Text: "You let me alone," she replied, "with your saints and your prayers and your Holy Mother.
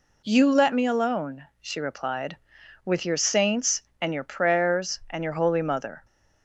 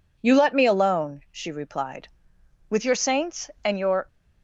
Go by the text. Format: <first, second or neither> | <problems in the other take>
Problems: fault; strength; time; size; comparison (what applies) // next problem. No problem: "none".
first | stops before "prayers and your Holy Mother"; at 4.0 s